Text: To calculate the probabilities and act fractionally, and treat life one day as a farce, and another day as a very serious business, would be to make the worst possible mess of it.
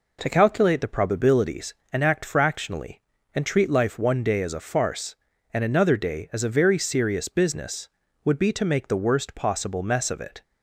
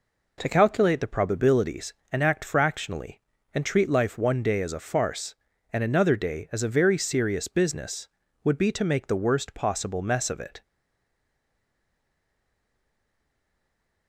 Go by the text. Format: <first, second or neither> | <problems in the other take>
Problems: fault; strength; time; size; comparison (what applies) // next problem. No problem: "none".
first | stays silent after the last word; strong; from 10.6 s on; 3.4 s long